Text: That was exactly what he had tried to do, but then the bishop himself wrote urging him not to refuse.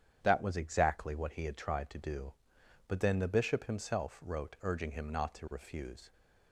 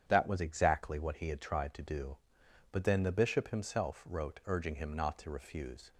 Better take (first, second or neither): neither